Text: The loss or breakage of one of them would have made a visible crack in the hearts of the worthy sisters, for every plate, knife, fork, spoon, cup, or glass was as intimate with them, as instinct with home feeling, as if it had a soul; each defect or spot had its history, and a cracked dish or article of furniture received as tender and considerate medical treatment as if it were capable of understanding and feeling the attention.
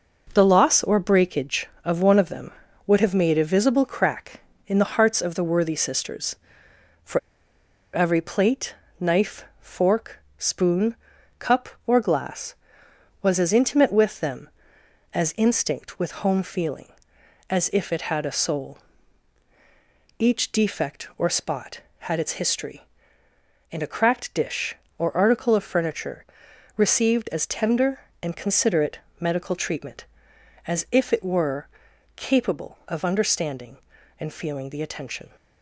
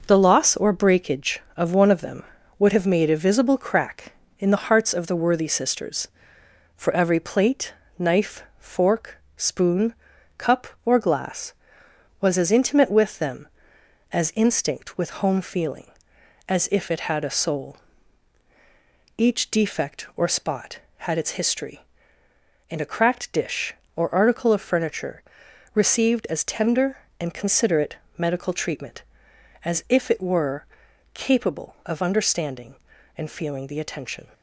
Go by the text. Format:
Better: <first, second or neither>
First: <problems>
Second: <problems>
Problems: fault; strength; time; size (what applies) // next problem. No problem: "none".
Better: second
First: pauses between "for" and "every"; noticeable; at 7.1 s; 0.75 s long // pauses between "furniture" and "received"; noticeable; at 26.2 s; 0.54 s long // pauses between "considerate" and "medical"; slight; at 28.9 s; 0.20 s long // pauses between "were" and "capable"; noticeable; at 31.6 s; 0.48 s long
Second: pauses between "furniture" and "received"; noticeable; at 25.2 s; 0.54 s long // pauses between "considerate" and "medical"; slight; at 27.9 s; 0.20 s long // pauses between "were" and "capable"; noticeable; at 30.6 s; 0.48 s long